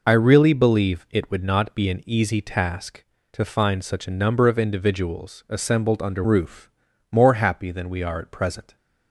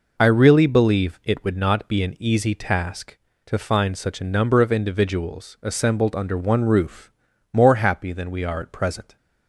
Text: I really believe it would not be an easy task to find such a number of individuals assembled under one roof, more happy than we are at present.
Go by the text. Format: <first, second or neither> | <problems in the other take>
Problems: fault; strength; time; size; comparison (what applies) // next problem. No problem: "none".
second | skips "one"; at 6.2 s